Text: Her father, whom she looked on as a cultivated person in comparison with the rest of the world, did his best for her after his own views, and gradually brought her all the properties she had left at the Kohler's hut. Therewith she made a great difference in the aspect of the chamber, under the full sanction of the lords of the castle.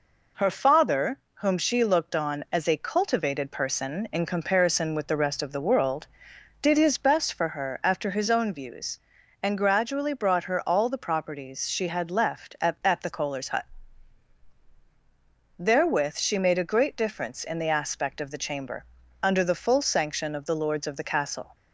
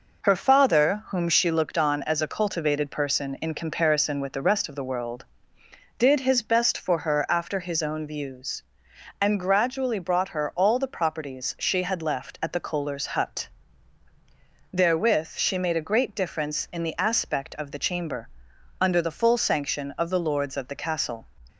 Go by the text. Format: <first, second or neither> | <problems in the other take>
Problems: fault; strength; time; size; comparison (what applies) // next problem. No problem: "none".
second | says "at" twice; at 12.8 s